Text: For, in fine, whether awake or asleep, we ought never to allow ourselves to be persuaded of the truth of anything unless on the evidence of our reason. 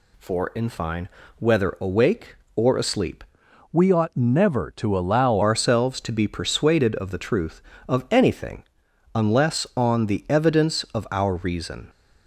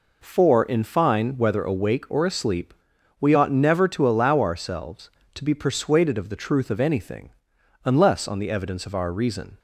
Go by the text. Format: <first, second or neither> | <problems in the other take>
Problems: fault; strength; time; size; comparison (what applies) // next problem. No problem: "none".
second | changes voice from "we" to "allow"; from 3.7 to 5.4 s; 1.7 s long // pauses between "anything" and "unless"; noticeable; at 8.6 s; 0.52 s long; noticeable in the second